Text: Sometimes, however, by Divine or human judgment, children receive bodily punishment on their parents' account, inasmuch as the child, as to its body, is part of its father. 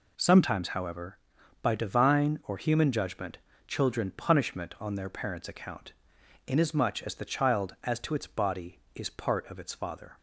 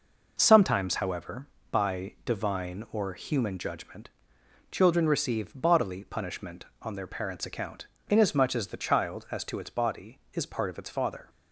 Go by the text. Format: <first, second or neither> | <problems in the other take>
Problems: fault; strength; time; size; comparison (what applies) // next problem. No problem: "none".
second | skips "receive bodily"; at 4.1 s